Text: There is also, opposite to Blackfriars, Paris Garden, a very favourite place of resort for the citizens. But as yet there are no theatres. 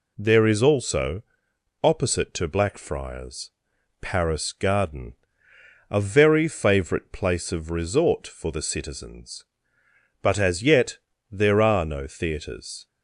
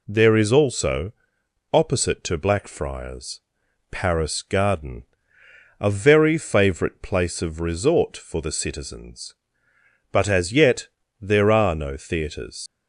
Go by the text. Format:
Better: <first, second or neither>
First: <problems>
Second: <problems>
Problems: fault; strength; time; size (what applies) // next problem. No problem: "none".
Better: first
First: pauses between "yet" and "there"; slight; at 10.9 s; 0.32 s long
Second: pauses between "yet" and "there"; slight; at 10.8 s; 0.32 s long // leaves "theatres" unfinished; at 12.6 s; 100 ms